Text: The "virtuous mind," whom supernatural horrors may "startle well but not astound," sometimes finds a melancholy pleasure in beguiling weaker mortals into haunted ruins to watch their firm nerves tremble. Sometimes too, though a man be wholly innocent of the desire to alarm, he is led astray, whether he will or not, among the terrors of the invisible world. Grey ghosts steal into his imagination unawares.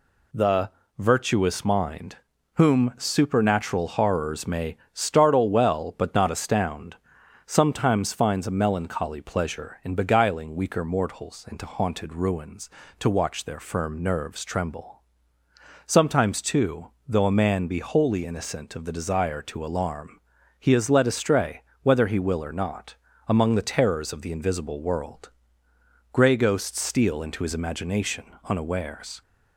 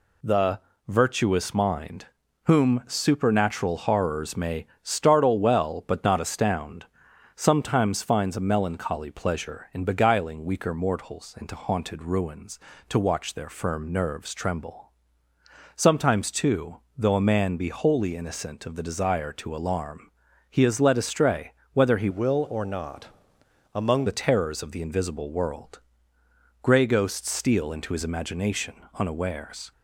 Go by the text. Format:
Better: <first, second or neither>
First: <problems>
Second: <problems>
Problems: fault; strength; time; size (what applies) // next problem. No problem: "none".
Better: first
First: pauses between "The" and "virtuous"; slight; at 0.6 s; 0.30 s long // pauses between "may" and "startle"; slight; at 4.7 s; 0.16 s long // pauses between "imagination" and "unawares"; slight; at 28.2 s; 0.18 s long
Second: pauses between "The" and "virtuous"; slight; at 0.5 s; 0.30 s long // pauses between "may" and "startle"; slight; at 4.6 s; 0.16 s long // changes voice from "will" to "among"; from 22.0 to 24.0 s; 2.0 s long // pauses between "imagination" and "unawares"; slight; at 28.7 s; 0.18 s long